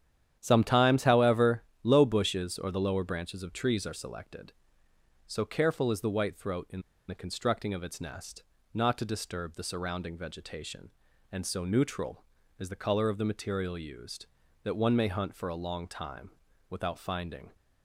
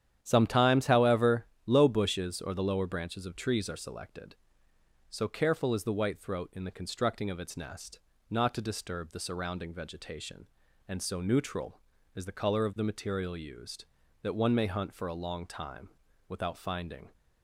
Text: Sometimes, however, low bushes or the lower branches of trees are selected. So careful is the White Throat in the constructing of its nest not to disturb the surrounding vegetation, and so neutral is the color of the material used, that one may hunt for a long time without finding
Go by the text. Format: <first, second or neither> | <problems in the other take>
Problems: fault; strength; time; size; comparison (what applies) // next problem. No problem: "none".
second | starts louder than the rest; strong; until 1.4 s; 10 dB; strong in the second // pauses between "in" and "the"; slight; at 6.8 s; 0.28 s long // pauses between "nest" and "not"; slight; at 8.4 s; 0.30 s long; slight in the second // pauses between "time" and "without"; at 16.3 s; 0.38 s long; also in the second